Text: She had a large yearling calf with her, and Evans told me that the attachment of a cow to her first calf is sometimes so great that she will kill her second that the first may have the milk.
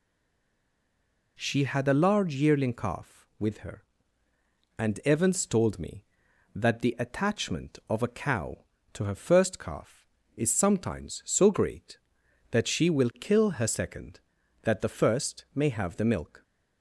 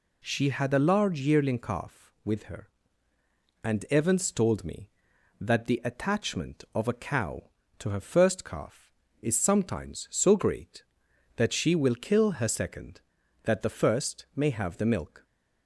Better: second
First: stays silent before the first word; noticeable; until 1.3 s; 1.3 s long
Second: none

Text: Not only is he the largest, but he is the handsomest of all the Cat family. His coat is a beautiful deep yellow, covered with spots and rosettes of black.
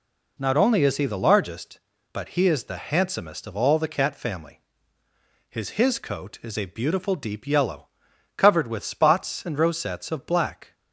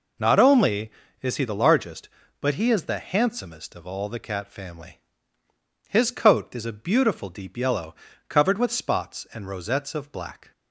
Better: second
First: says "His" twice; at 5.6 s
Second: none

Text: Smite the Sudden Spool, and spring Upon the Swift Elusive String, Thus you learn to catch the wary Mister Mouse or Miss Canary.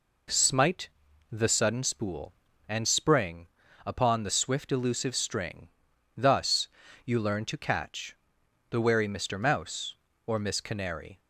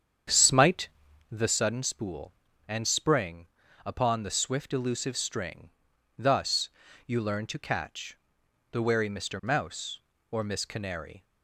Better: first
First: pauses between "Smite" and "the"; at 0.8 s; 0.42 s long // pauses between "spring" and "Upon"; at 3.4 s; 0.40 s long // pauses between "Thus" and "you"; at 6.6 s; 0.38 s long // pauses between "catch" and "the"; noticeable; at 8.1 s; 0.52 s long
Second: starts louder than the rest; strong; until 1.3 s; 8 dB // pauses between "Smite" and "the"; at 0.8 s; 0.42 s long // pauses between "spring" and "Upon"; at 3.4 s; 0.40 s long // pauses between "Thus" and "you"; at 6.6 s; 0.38 s long // pauses between "catch" and "the"; noticeable; at 8.1 s; 0.52 s long

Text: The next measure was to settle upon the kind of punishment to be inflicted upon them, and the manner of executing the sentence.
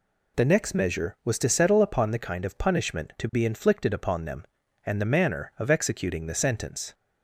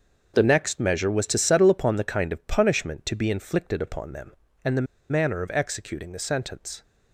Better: first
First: none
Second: starts louder than the rest; until 1.3 s; 6.5 dB // pauses between "the" and "manner"; slight; at 4.8 s; 0.26 s long

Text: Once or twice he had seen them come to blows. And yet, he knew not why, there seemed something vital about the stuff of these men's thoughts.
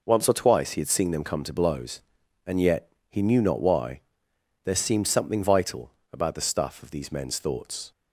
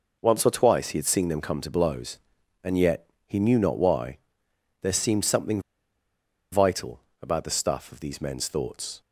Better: first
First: pauses between "vital" and "about"; slight; at 5.9 s; 0.22 s long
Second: pauses between "something" and "vital"; noticeable; at 5.6 s; 0.91 s long // pauses between "vital" and "about"; slight; at 7.0 s; 0.22 s long

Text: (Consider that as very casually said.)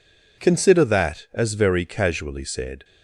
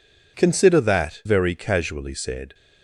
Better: first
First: none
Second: skips "as"; at 1.2 s

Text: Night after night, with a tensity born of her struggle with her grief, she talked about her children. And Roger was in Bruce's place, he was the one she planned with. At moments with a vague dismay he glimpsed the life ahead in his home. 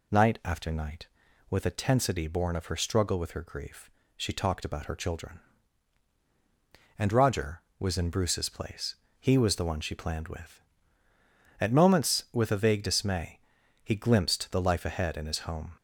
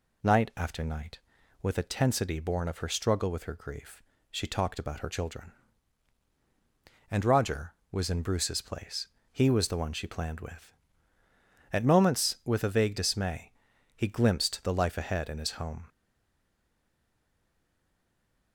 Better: first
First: pauses between "dismay" and "he"; noticeable; at 13.3 s; 0.46 s long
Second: pauses between "dismay" and "he"; noticeable; at 13.5 s; 0.46 s long // stays silent after the last word; strong; from 15.8 s on; 2.7 s long

